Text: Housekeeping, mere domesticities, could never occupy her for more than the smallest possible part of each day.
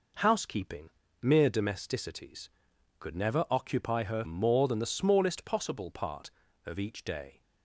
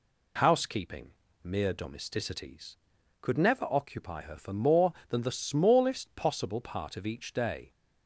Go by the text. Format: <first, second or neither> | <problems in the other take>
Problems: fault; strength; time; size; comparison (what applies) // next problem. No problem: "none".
second | skips "for"; at 4.2 s